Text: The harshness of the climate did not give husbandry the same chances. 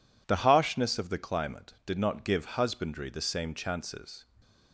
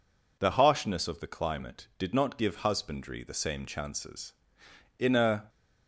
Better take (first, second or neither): first